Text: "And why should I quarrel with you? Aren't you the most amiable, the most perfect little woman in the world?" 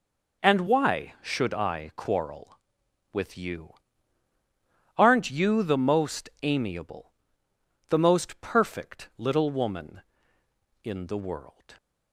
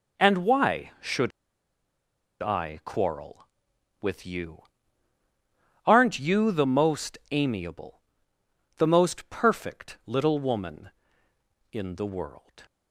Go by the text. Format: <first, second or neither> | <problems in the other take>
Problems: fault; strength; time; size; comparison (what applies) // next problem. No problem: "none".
first | pauses between "should" and "I"; at 1.3 s; 1.1 s long